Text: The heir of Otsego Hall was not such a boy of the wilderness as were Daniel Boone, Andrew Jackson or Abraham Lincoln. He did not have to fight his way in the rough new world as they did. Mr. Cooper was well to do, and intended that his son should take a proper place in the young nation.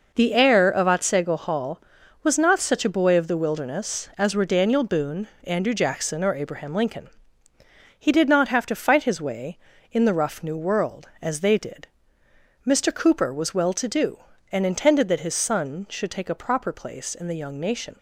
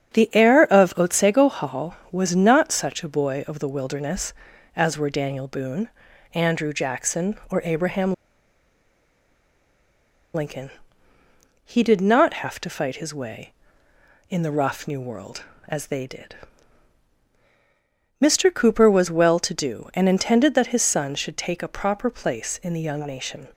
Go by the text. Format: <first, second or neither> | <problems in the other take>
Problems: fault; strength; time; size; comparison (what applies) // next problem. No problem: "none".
first | starts louder than the rest; strong; until 1.2 s; 8 dB // pauses between "Abraham" and "Lincoln"; strong; at 8.1 s; 2.2 s long